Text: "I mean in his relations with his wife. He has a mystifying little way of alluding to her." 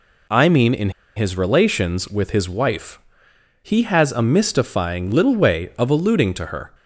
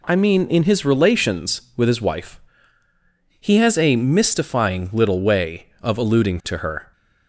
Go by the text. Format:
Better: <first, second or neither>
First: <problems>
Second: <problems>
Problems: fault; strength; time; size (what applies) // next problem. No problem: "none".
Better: second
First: pauses between "in" and "his"; slight; at 0.8 s; 0.26 s long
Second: none